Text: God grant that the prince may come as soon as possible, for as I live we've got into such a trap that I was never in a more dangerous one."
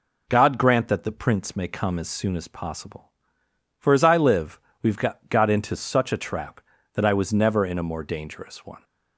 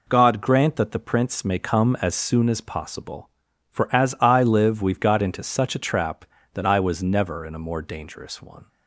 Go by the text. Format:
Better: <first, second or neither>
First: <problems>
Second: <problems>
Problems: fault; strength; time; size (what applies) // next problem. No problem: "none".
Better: second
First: pauses between "live" and "we've"; slight; at 4.5 s; 0.22 s long // says "got" twice; at 5.2 s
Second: none